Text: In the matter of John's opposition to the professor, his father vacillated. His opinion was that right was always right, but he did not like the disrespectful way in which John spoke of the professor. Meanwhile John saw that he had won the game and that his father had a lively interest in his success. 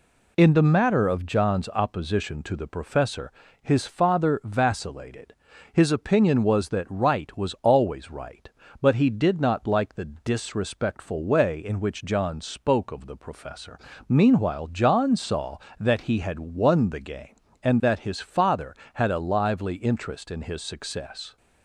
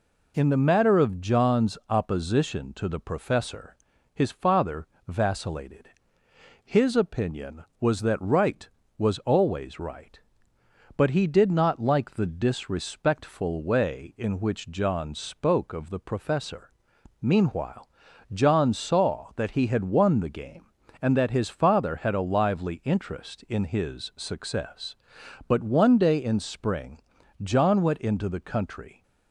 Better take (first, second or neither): first